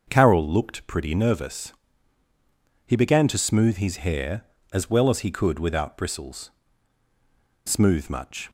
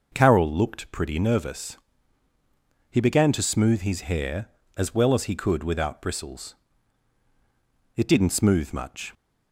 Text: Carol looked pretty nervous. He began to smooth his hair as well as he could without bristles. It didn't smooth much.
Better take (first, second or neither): second